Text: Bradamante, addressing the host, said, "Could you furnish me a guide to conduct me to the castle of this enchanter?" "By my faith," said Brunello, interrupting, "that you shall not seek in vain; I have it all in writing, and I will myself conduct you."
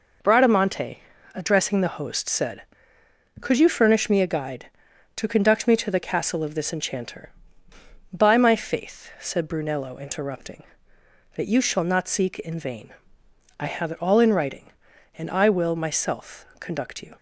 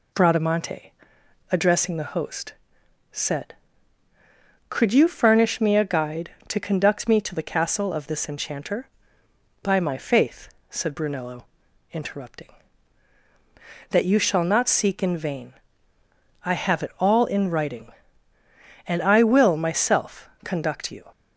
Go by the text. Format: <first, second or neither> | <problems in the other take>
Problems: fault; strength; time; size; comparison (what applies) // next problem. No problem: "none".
neither | none